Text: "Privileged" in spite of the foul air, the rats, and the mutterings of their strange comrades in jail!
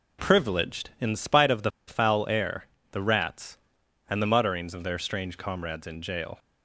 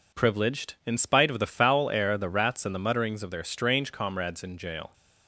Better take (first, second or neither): second